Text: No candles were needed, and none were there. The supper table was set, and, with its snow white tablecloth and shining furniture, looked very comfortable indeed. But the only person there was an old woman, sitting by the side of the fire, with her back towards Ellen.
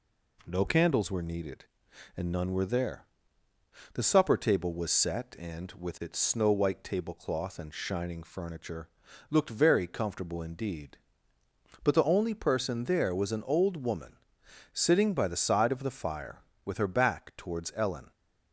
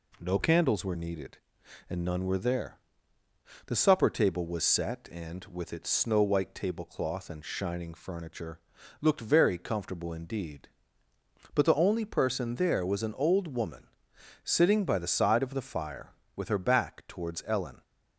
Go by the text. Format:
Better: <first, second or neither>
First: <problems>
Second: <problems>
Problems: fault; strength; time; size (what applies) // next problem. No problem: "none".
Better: neither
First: none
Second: none